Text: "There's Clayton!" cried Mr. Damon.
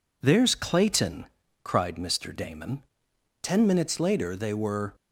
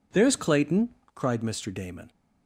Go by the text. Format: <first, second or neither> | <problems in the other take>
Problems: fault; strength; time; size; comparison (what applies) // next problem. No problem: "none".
second | goes on to say "Ten minutes later they were"; from 3.4 s on; 1.5 s long